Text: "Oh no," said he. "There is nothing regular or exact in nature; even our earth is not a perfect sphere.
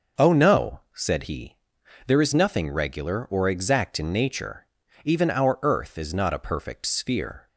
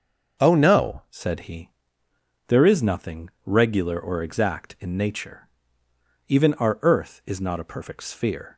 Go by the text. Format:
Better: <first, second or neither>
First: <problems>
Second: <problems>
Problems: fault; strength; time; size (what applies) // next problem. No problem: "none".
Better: first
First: starts louder than the rest; noticeable; until 1.3 s; 6 dB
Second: starts louder than the rest; noticeable; until 1.4 s; 6 dB // changes voice at "said"; from 1.1 s on; 7.4 s long